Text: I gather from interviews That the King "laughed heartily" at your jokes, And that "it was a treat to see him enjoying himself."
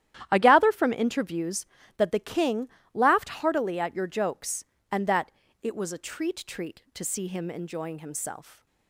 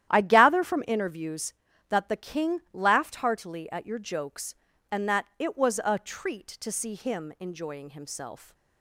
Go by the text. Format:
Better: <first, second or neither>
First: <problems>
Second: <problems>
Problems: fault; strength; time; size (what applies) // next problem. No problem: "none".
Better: second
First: starts louder than the rest; strong; until 1.3 s; 11.5 dB // pauses between "King" and "laughed"; slight; at 2.6 s; 0.24 s long // pauses between "that" and "it"; slight; at 5.2 s; 0.32 s long // says "treat" twice; at 6.4 s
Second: starts louder than the rest; strong; until 1.1 s; 11.5 dB